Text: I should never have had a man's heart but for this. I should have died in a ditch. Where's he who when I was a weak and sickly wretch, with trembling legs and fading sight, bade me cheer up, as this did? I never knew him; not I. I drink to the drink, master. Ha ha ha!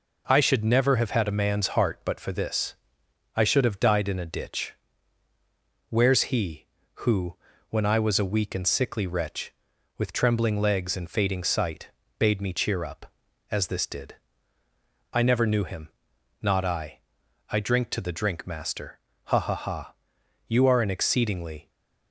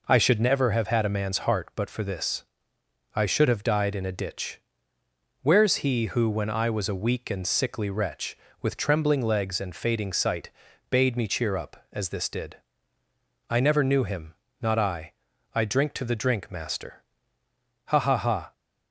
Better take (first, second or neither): second